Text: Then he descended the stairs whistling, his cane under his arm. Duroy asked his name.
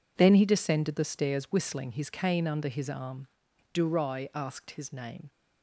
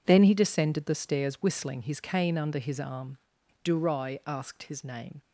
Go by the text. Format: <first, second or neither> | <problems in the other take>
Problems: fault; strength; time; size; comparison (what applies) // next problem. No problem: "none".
neither | none